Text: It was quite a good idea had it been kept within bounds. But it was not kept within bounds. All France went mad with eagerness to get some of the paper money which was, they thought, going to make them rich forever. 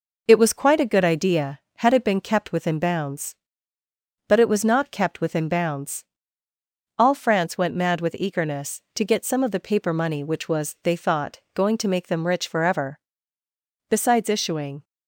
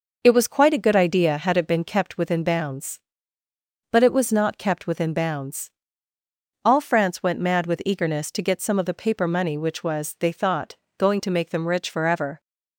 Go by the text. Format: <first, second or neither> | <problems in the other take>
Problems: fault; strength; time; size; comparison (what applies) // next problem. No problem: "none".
second | goes on to say "Besides issuing"; noticeable; from 13.8 s on; 0.94 s long